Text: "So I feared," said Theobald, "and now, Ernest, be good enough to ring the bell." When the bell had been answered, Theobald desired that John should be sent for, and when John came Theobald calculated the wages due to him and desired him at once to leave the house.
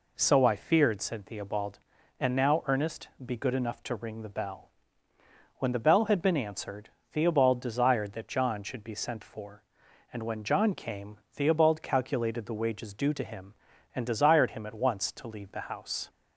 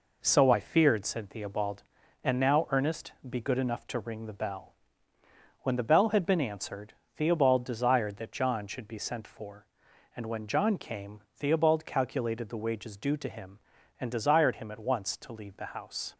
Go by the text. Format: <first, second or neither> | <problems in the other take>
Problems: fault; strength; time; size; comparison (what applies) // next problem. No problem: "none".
first | gets quieter; noticeable; throughout; 5.5 dB // pauses between "came" and "Theobald"; slight; at 11.2 s; 0.16 s long; slight in the first